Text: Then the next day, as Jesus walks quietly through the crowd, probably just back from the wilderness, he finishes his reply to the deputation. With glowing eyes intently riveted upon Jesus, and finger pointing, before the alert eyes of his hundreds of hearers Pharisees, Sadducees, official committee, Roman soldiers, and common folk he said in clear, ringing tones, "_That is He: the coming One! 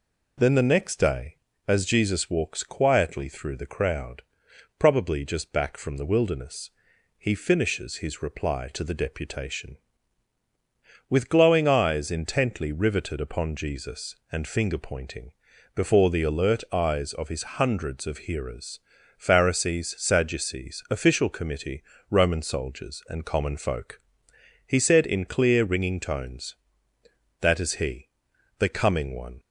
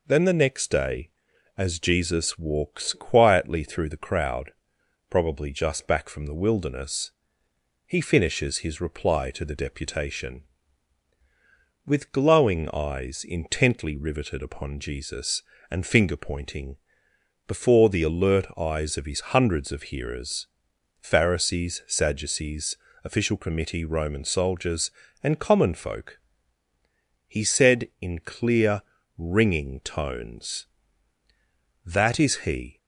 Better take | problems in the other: first | pauses between "hearers" and "Pharisees"; noticeable; at 20.4 s; 0.52 s long; also in the first // pauses between "folk" and "he"; at 26.1 s; 1.1 s long; noticeable in the first // stops before "the coming One"; at 32.7 s

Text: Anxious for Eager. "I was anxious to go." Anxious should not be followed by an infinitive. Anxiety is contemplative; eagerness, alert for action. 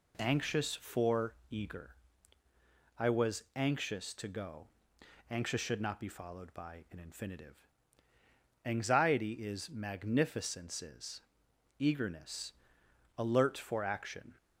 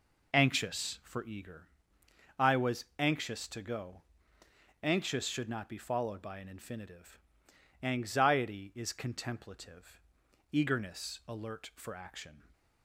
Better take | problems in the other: second | pauses between "for" and "Eager"; slight; at 1.3 s; 0.16 s long // says "magnificences" for "contemplative"; at 9.6 s

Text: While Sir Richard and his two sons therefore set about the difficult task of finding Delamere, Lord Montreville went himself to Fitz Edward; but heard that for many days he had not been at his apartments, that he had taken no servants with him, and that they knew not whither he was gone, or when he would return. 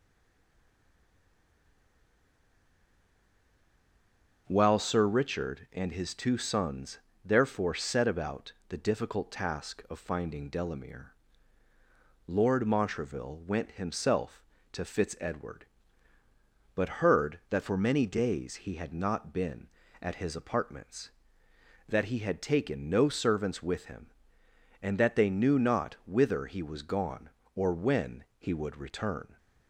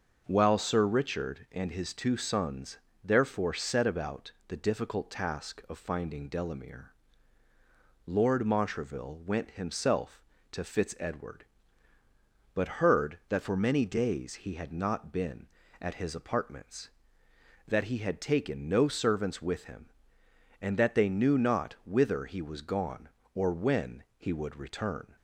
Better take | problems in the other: second | stays silent before the first word; strong; until 4.4 s; 4.4 s long // pauses between "sons" and "therefore"; slight; at 6.9 s; 0.26 s long; slight in the second // pauses between "about" and "the"; slight; at 8.5 s; 0.16 s long; slight in the second

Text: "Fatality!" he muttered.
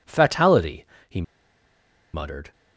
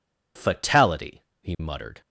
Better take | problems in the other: second | pauses between "he" and "muttered"; noticeable; at 1.2 s; 0.91 s long

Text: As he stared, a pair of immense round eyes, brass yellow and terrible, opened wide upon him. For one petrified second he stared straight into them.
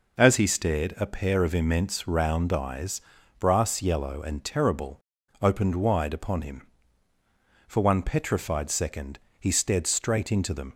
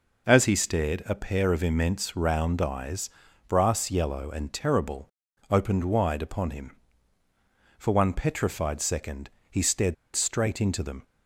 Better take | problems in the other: first | pauses between "second" and "he"; slight; at 9.2 s; 0.22 s long; slight in the first // pauses between "stared" and "straight"; slight; at 9.9 s; 0.20 s long

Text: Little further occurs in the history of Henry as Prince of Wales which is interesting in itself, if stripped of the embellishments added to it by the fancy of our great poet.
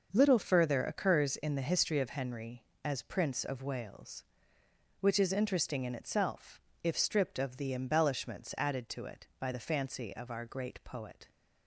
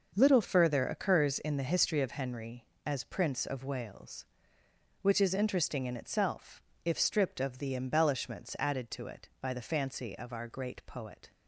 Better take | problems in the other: neither | starts louder than the rest; noticeable; the same in both

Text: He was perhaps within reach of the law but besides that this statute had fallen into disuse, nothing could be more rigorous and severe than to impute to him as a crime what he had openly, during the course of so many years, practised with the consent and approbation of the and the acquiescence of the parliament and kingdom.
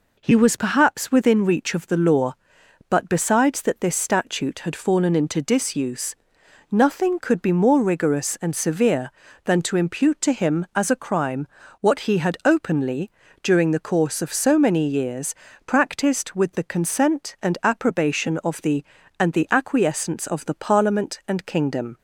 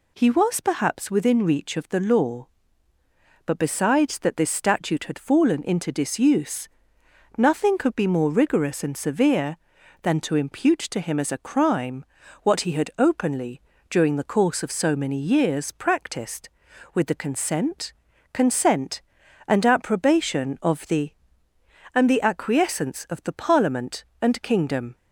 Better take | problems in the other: first | pauses between "crime" and "what"; slight; at 12.0 s; 0.34 s long; slight in the first // says "consent" twice; at 18.3 s

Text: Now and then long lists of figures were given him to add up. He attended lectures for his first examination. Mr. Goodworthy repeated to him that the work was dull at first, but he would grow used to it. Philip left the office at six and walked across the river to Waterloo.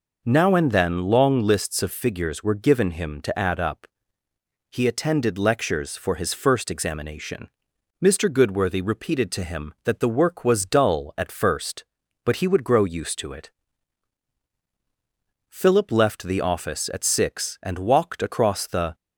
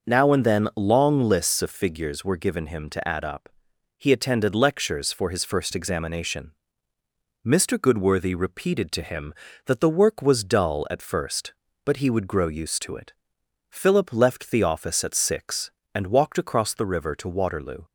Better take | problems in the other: second | stops before "river to Waterloo"; at 18.9 s

